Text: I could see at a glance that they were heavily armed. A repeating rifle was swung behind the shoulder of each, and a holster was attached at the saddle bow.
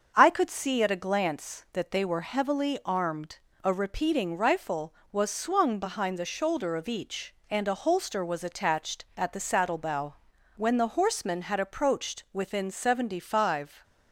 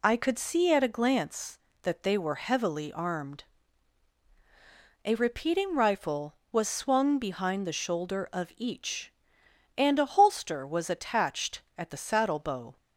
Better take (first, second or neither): second